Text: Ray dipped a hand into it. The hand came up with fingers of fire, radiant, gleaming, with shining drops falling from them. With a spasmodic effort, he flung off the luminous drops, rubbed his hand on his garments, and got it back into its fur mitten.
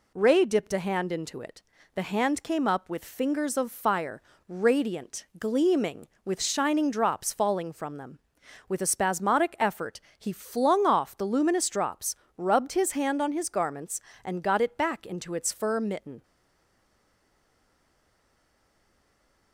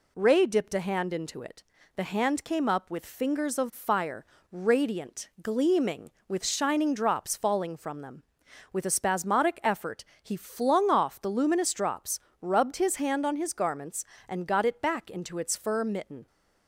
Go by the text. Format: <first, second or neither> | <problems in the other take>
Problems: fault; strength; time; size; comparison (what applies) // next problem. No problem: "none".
second | stays silent after the last word; strong; from 16.2 s on; 3.3 s long